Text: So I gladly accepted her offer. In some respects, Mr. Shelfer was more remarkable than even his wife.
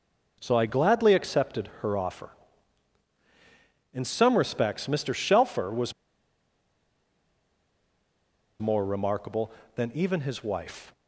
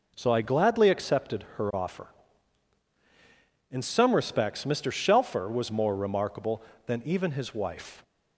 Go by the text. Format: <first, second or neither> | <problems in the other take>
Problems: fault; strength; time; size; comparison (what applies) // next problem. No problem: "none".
second | pauses between "was" and "more"; strong; at 5.9 s; 2.6 s long